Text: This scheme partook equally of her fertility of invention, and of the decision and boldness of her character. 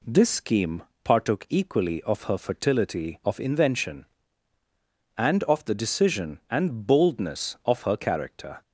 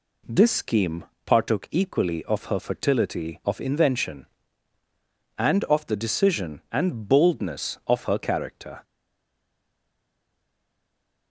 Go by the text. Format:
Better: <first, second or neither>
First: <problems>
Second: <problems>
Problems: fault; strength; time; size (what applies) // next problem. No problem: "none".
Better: first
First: pauses between "scheme" and "partook"; slight; at 0.8 s; 0.22 s long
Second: pauses between "scheme" and "partook"; slight; at 1.0 s; 0.22 s long // stays silent after the last word; from 8.8 s on; 2.4 s long